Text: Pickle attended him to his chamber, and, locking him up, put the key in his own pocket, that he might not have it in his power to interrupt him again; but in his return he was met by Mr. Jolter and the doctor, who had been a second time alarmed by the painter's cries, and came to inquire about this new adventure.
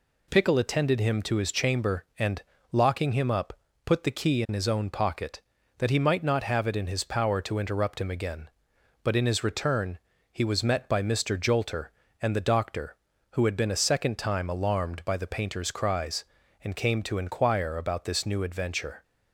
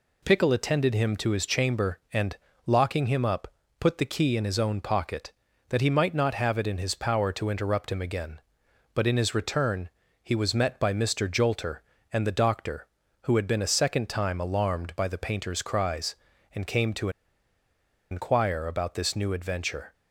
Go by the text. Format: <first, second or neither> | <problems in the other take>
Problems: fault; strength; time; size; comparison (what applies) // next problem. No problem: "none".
first | pauses between "return" and "he"; slight; at 9.8 s; 0.34 s long; slight in the first // pauses between "to" and "inquire"; at 17.0 s; 1.0 s long